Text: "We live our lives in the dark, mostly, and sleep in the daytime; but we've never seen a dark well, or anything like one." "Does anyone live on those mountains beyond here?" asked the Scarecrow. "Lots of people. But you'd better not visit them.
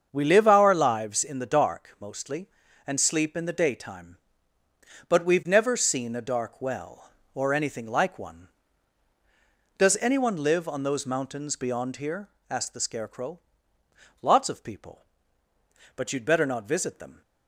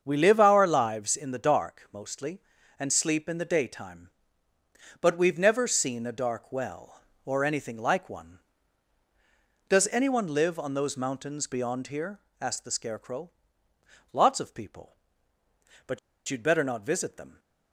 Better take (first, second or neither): first